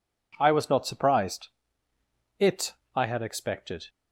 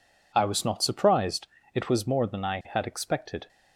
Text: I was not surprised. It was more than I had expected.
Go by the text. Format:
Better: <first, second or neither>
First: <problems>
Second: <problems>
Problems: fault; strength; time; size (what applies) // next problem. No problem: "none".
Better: second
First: skips "was more than"; at 2.8 s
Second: none